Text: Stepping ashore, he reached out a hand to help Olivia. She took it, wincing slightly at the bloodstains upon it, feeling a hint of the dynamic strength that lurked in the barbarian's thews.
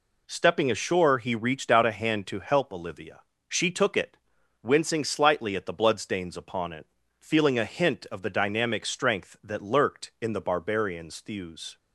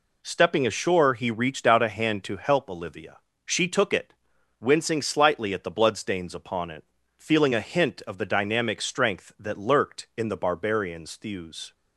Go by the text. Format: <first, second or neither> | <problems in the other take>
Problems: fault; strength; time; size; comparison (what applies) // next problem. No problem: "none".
neither | none